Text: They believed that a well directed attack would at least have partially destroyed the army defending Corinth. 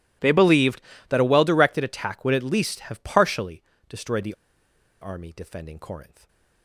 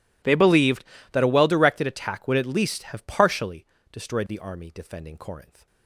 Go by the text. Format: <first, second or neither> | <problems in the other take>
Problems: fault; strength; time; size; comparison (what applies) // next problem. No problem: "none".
second | pauses between "partially" and "destroyed"; slight; at 3.6 s; 0.26 s long; slight in the second // pauses between "the" and "army"; noticeable; at 4.3 s; 0.68 s long // stays silent after the last word; slight; from 6.0 s on; 0.6 s long